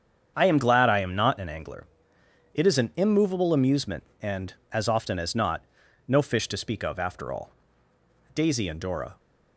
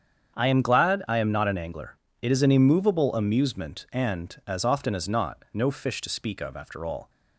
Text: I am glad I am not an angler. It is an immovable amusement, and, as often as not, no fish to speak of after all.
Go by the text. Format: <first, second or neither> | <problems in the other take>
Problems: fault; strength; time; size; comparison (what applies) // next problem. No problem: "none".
second | starts louder than the rest; strong; until 1.3 s; 7.5 dB; strong in the second // goes on to say "Daisy and Dora"; noticeable; from 8.3 s on; 0.80 s long